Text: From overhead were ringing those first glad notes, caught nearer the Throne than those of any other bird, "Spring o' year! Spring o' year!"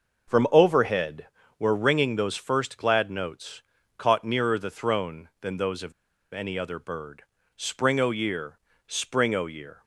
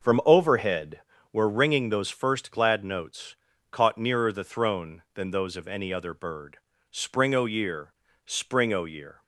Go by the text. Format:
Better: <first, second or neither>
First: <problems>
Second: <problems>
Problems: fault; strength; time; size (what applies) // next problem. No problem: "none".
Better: second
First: starts louder than the rest; noticeable; until 1.6 s; 6 dB // pauses between "of" and "any"; at 5.9 s; 0.41 s long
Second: starts louder than the rest; noticeable; until 1.4 s; 6 dB